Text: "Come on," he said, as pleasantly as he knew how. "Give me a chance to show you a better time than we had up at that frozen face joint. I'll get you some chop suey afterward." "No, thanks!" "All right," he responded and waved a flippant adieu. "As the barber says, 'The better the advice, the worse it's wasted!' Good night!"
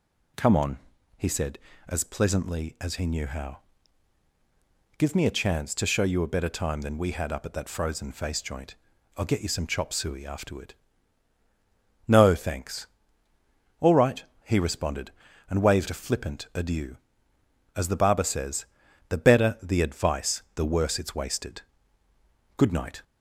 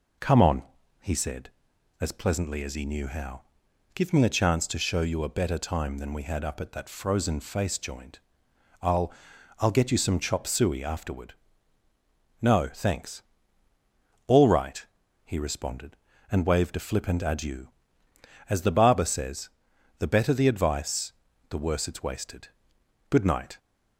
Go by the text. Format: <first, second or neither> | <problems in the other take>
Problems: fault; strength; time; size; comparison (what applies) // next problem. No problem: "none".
first | says "I'll" twice; at 9.5 s